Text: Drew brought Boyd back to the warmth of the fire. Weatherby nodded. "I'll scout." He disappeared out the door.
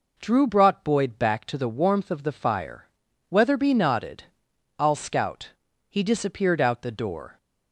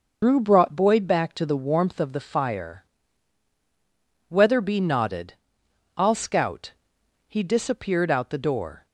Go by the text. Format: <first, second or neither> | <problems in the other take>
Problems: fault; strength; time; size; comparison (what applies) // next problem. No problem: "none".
first | loses the start of "Drew"; at 0.2 s; 115 ms